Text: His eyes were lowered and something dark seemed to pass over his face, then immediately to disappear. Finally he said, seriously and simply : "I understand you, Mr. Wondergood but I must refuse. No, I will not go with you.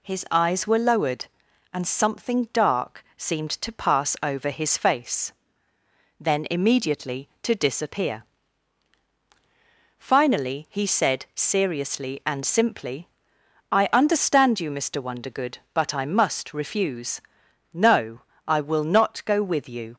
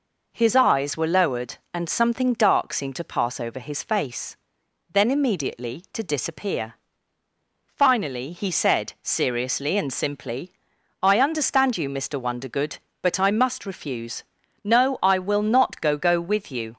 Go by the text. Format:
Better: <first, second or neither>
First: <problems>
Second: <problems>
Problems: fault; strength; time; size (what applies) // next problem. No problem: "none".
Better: first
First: none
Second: says "go" twice; at 15.9 s